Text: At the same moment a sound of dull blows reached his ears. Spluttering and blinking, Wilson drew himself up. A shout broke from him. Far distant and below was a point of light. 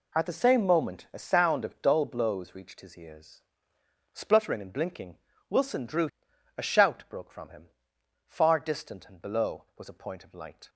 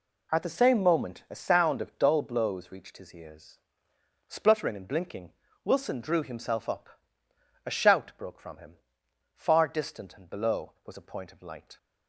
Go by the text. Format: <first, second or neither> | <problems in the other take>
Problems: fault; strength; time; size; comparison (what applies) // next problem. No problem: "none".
second | skips "himself up"; at 6.3 s